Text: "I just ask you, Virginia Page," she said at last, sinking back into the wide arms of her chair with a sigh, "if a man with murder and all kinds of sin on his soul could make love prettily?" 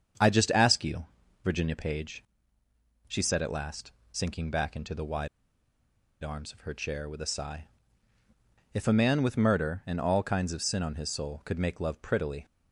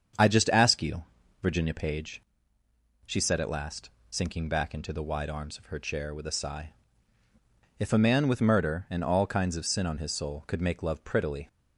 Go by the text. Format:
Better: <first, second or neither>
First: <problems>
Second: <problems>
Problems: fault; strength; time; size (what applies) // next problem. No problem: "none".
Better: second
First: starts louder than the rest; strong; until 1.5 s; 7.5 dB // pauses between "wide" and "arms"; noticeable; at 5.2 s; 0.94 s long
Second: starts louder than the rest; strong; until 1.5 s; 7.5 dB